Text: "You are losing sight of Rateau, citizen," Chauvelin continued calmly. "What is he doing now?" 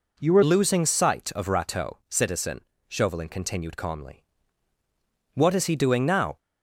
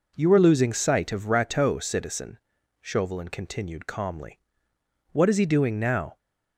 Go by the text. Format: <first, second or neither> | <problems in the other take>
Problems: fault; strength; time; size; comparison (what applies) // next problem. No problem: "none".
second | changes voice at "losing"; from 0.4 s on; 5.9 s long